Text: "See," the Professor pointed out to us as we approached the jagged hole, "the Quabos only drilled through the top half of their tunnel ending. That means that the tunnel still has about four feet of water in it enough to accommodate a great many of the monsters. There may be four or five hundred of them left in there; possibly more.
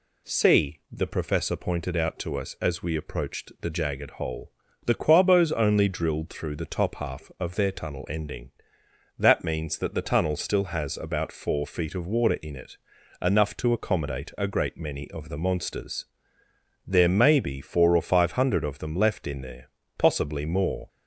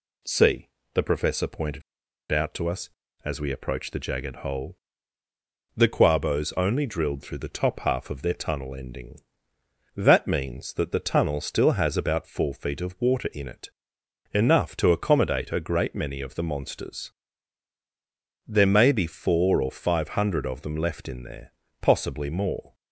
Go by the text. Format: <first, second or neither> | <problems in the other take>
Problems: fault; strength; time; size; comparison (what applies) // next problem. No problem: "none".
first | pauses between "pointed" and "out"; noticeable; at 1.8 s; 0.50 s long // pauses between "it" and "enough"; noticeable; at 13.7 s; 0.64 s long; also in the first